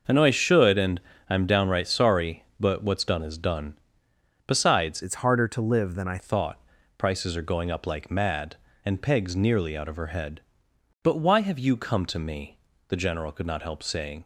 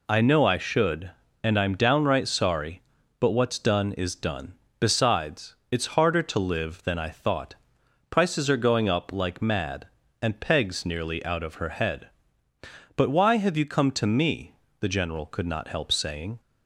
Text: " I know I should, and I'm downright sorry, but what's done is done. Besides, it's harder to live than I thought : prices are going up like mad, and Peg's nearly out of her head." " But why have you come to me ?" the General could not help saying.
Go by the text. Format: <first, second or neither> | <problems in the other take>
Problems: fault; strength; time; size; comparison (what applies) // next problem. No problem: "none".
second | pauses between "and" and "I'm"; slight; at 0.9 s; 0.28 s long // changes voice from "it's" to "I"; from 5.0 to 6.1 s; 1.1 s long